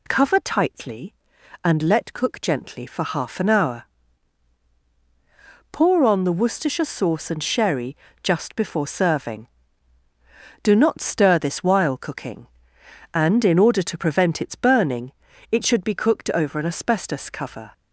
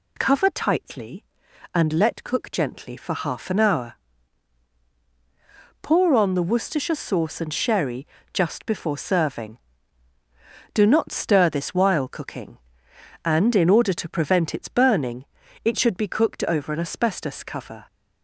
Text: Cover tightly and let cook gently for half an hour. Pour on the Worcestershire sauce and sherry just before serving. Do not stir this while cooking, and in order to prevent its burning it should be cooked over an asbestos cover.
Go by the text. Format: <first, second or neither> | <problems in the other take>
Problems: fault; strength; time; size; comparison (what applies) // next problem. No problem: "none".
neither | pauses between "sherry" and "just"; slight; the same in both // pauses between "burning" and "it"; the same in both